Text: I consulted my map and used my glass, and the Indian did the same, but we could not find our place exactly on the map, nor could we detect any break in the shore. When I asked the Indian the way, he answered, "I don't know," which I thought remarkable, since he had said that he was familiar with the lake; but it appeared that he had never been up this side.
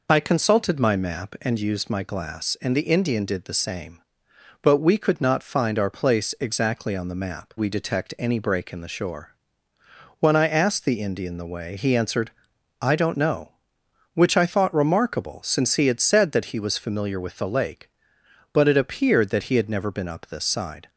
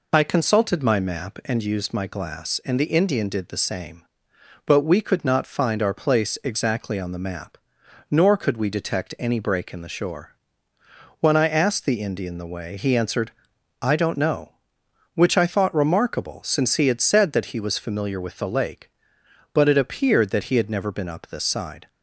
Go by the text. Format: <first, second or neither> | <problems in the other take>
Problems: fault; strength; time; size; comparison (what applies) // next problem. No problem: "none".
second | skips "nor could"; at 7.5 s